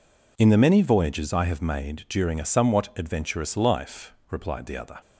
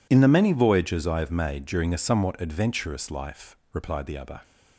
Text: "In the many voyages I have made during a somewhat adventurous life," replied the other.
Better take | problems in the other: neither | none

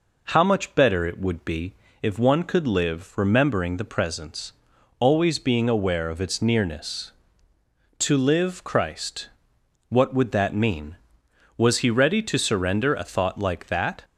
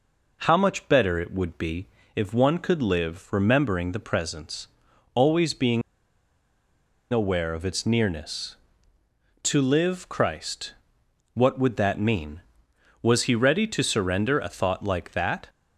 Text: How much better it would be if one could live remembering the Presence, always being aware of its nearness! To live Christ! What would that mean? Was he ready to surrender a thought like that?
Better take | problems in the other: first | pauses between "be" and "if"; slight; at 1.8 s; 0.28 s long; slight in the first // pauses between "being" and "aware"; strong; at 5.8 s; 1.3 s long

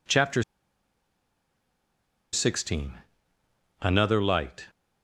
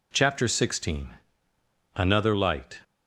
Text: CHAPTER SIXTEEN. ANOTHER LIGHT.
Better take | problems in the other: second | pauses between "CHAPTER" and "SIXTEEN"; strong; at 0.4 s; 1.8 s long

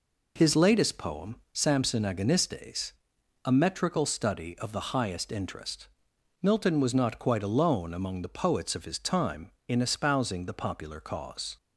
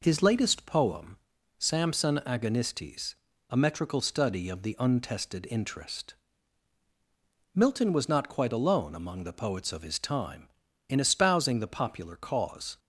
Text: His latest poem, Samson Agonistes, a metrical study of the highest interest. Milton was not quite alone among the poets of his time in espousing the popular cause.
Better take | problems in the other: first | says "untested" for "highest"; at 4.7 s

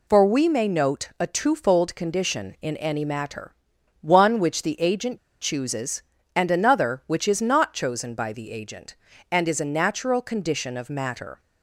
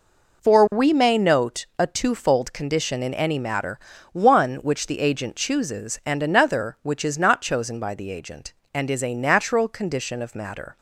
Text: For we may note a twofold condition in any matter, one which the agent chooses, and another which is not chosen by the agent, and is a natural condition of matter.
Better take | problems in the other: second | pauses between "agent" and "chooses"; slight; at 5.1 s; 0.23 s long

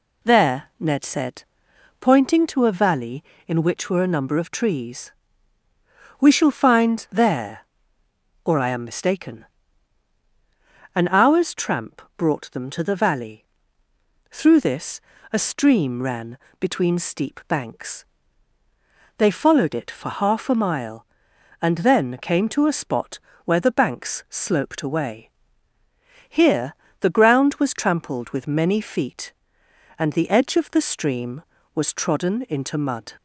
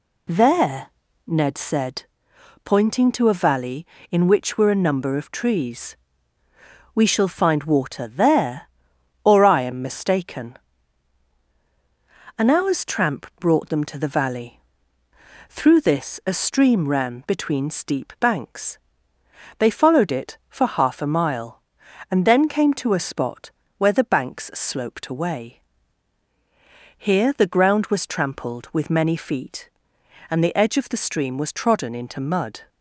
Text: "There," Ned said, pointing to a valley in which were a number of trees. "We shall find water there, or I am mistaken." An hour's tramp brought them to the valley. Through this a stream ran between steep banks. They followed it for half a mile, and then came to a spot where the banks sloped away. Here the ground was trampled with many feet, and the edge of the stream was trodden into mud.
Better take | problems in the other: second | skips "water"; at 7.0 s // pauses between "tramp" and "brought"; slight; at 12.0 s; 0.16 s long // pauses between "this" and "a"; slight; at 14.9 s; 0.32 s long // pauses between "ran" and "between"; slight; at 16.3 s; 0.22 s long // pauses between "spot" and "where"; slight; at 23.1 s; 0.26 s long; slight in the second // pauses between "Here" and "the"; slight; at 26.7 s; 0.26 s long

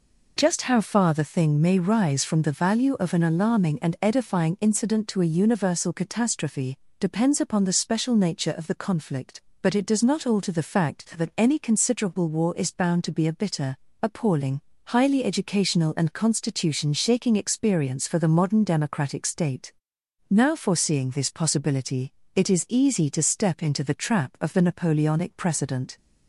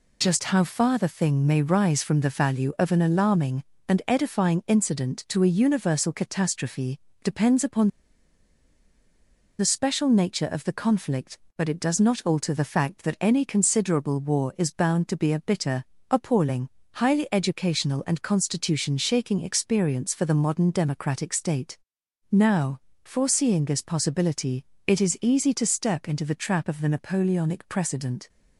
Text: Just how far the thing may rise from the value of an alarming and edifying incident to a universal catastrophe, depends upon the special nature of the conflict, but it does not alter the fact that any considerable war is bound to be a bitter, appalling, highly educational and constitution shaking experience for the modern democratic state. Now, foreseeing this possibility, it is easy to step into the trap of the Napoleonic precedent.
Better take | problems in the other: first | pauses between "upon" and "the"; strong; at 7.8 s; 1.7 s long

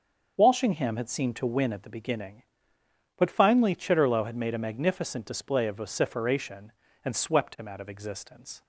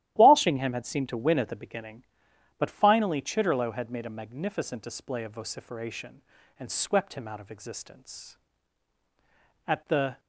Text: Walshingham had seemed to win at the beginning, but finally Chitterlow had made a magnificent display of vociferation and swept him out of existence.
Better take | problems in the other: first | starts louder than the rest; strong; until 1.1 s; 13 dB; also in the first // goes on to say "At the"; from 9.6 s on; 0.52 s long

